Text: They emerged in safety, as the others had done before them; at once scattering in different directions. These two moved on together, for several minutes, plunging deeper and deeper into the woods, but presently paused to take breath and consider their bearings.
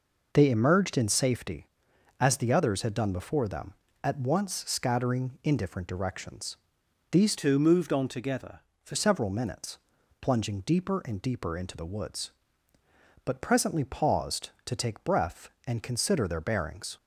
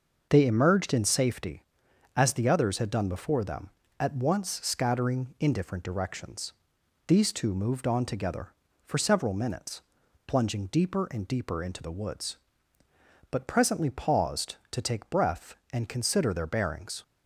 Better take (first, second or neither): second